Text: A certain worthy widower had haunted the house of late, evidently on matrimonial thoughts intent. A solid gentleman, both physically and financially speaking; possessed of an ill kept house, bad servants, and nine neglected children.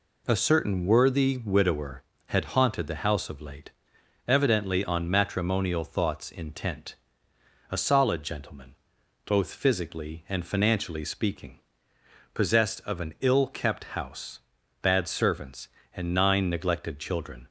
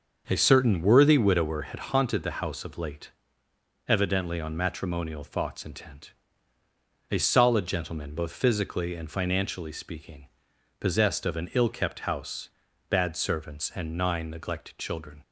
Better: first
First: none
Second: starts louder than the rest; until 1.5 s; 6.5 dB

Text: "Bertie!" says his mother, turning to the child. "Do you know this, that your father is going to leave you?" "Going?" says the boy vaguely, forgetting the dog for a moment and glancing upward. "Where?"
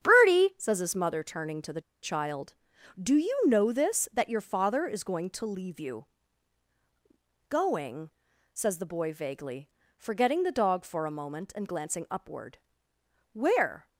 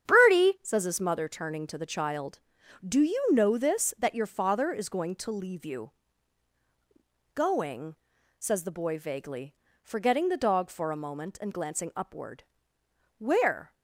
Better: second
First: starts louder than the rest; strong; until 1.0 s; 8.5 dB // pauses between "the" and "child"; slight; at 1.8 s; 0.22 s long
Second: starts louder than the rest; strong; until 1.1 s; 8.5 dB

